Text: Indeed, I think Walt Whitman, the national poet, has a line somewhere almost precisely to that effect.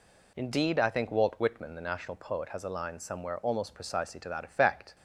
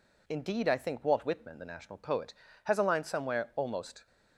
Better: first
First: none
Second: stops before "precisely to that effect"; at 4.0 s

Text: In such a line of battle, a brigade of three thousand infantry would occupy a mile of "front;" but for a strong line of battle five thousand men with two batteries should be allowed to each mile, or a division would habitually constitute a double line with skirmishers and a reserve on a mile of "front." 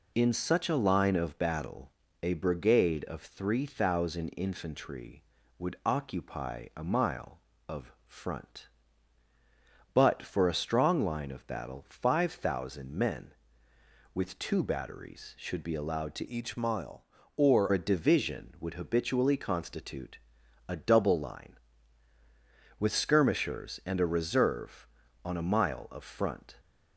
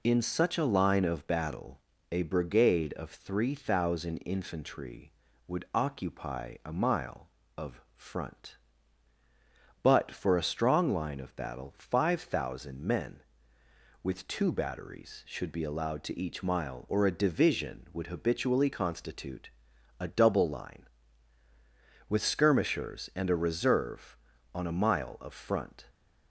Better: second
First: pauses between "of" and "front"; slight; at 7.9 s; 0.16 s long // changes voice from "each" to "or"; from 16.2 to 17.6 s; 1.4 s long // pauses between "constitute" and "a"; noticeable; at 20.1 s; 0.50 s long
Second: pauses between "of" and "front"; slight; at 7.8 s; 0.16 s long // pauses between "constitute" and "a"; noticeable; at 19.4 s; 0.50 s long

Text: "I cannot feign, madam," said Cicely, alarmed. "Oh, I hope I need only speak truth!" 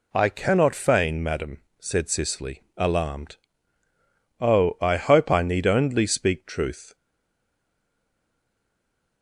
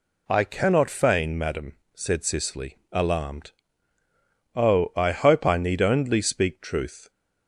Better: second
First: stays silent after the last word; from 6.9 s on; 2.3 s long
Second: none

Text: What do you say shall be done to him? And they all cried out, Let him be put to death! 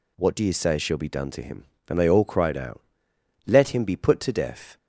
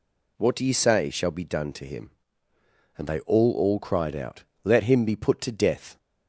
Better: first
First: none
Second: says "all" twice; at 3.5 s

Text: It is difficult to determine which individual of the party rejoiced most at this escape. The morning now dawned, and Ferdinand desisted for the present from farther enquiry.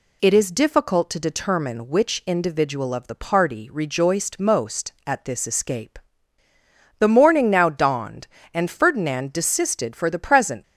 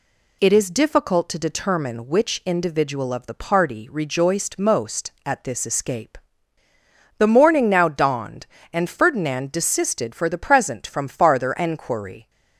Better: second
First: stops before "from farther enquiry"; at 10.6 s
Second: none

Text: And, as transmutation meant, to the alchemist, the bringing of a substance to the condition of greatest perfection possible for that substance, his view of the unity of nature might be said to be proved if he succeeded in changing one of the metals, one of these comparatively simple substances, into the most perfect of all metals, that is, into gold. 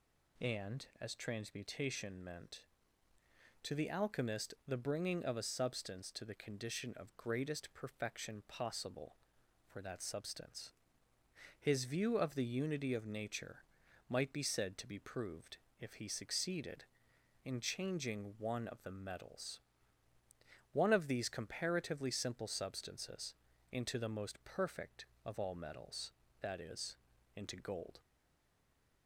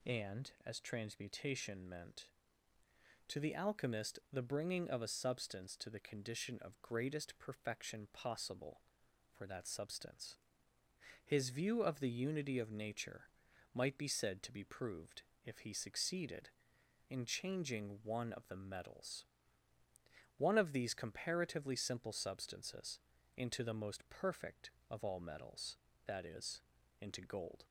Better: second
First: pauses between "nature" and "might"; noticeable; at 13.6 s; 0.46 s long // pauses between "proved" and "if"; slight; at 15.5 s; 0.24 s long // stays silent after the last word; from 28.0 s on; 1.0 s long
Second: pauses between "nature" and "might"; noticeable; at 13.2 s; 0.46 s long // pauses between "proved" and "if"; slight; at 15.2 s; 0.24 s long

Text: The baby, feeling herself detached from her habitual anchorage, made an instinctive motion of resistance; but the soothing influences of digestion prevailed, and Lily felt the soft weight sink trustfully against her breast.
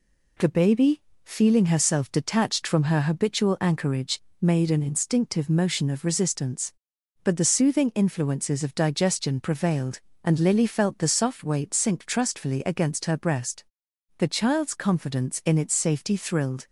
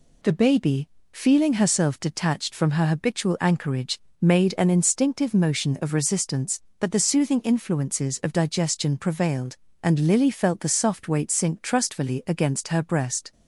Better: second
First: goes on to say "The child's confidence in its safety thrilled"; strong; from 14.1 s on; 2.4 s long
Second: none

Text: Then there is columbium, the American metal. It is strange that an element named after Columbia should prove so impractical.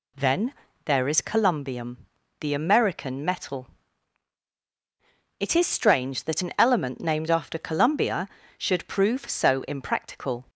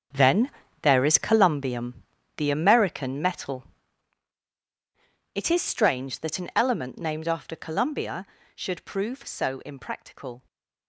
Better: first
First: pauses between "Then" and "there"; slight; at 0.5 s; 0.32 s long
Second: gets quieter; strong; throughout; 12.5 dB // pauses between "Then" and "there"; slight; at 0.4 s; 0.32 s long

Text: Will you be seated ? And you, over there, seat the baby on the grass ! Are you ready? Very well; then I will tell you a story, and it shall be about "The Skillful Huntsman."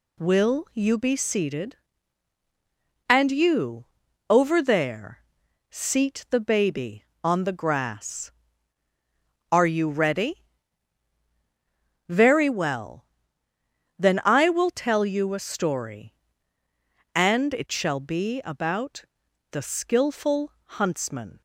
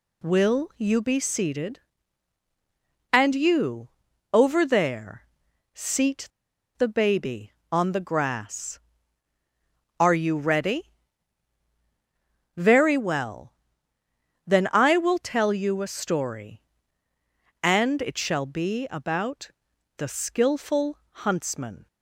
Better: first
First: pauses between "about" and "The"; noticeable; at 19.0 s; 0.48 s long // pauses between "Skillful" and "Huntsman"; slight; at 20.5 s; 0.24 s long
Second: pauses between "seat" and "the"; noticeable; at 6.2 s; 0.50 s long // pauses between "about" and "The"; noticeable; at 19.5 s; 0.48 s long // pauses between "Skillful" and "Huntsman"; slight; at 20.9 s; 0.24 s long

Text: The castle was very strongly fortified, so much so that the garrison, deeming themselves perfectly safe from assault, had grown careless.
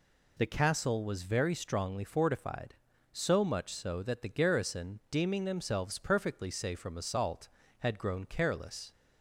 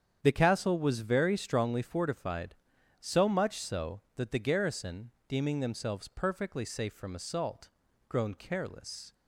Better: first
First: none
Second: starts louder than the rest; strong; until 1.2 s; 8.5 dB // skips "had"; at 7.8 s

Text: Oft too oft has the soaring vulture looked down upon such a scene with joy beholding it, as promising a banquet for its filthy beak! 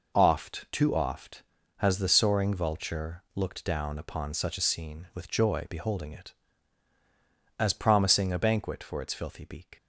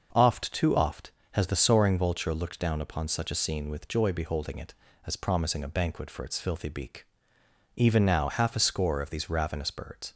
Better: first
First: none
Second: goes on to say "Even now half a score of these ravenous birds"; strong; from 7.7 s on; 2.3 s long

